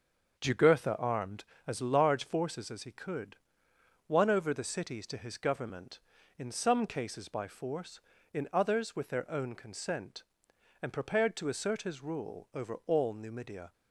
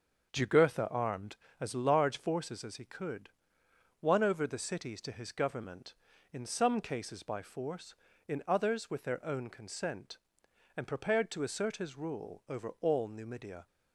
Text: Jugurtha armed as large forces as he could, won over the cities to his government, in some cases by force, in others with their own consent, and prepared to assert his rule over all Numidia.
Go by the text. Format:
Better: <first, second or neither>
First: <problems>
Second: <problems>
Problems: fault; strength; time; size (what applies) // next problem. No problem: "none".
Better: neither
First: starts louder than the rest; noticeable; until 1.4 s; 6 dB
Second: starts louder than the rest; until 1.3 s; 6.5 dB